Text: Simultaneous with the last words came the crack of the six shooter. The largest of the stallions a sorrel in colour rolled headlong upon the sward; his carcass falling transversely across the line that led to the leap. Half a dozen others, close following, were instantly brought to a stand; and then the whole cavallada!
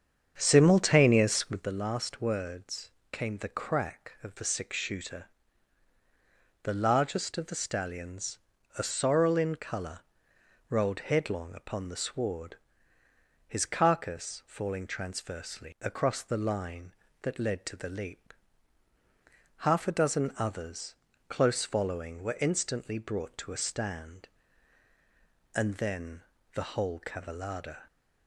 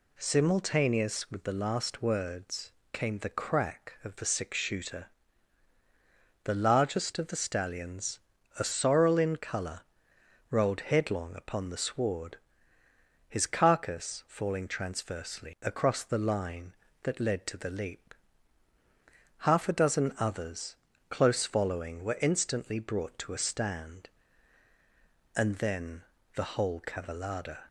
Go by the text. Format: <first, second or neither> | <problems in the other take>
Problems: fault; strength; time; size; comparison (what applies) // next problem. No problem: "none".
second | starts louder than the rest; strong; until 1.7 s; 7.5 dB // pauses between "words" and "came"; slight; at 2.9 s; 0.20 s long; slight in the second // pauses between "stallions" and "a"; at 8.3 s; 0.40 s long; also in the second // pauses between "colour" and "rolled"; noticeable; at 10.0 s; 0.68 s long; noticeable in the second // pauses between "then" and "the"; slight; at 26.2 s; 0.32 s long; slight in the second